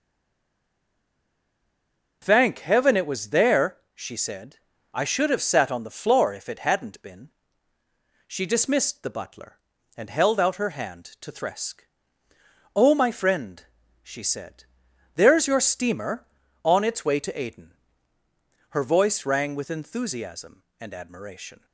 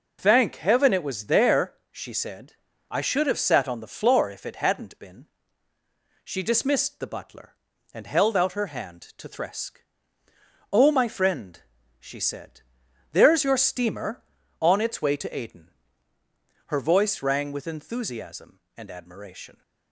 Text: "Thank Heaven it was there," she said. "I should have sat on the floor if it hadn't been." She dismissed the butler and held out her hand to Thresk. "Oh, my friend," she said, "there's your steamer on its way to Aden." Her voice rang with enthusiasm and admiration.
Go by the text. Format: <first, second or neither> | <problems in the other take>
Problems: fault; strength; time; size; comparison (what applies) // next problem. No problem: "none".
second | stays silent before the first word; until 2.2 s; 2.2 s long